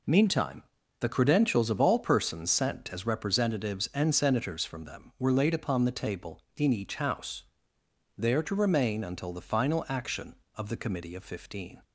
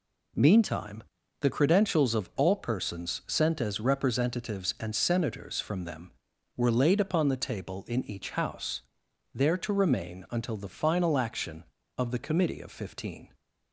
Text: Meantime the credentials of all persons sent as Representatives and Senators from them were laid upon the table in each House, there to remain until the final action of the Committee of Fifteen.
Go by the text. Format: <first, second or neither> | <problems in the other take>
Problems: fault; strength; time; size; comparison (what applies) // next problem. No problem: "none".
neither | pauses between "Meantime" and "the"; the same in both